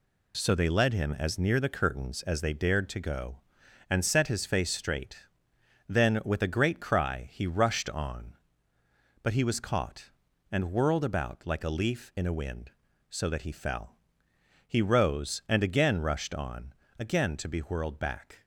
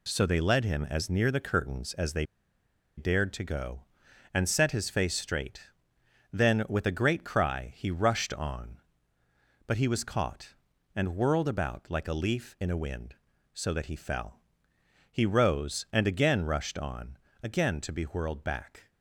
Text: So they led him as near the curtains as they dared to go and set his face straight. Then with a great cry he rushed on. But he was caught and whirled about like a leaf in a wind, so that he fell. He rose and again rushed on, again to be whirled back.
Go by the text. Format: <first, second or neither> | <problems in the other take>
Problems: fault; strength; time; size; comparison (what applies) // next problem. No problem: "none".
first | pauses between "they" and "dared"; noticeable; at 2.2 s; 0.72 s long